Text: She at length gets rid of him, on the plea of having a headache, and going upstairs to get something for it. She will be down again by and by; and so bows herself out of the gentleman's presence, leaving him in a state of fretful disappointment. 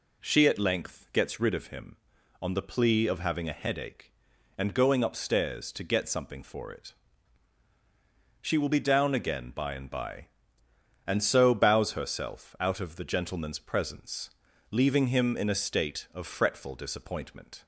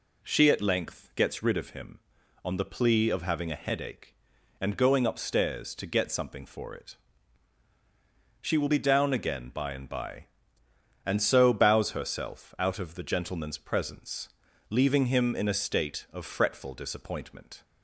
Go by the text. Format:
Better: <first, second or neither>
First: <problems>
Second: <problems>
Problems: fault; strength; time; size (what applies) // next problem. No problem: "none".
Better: neither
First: none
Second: none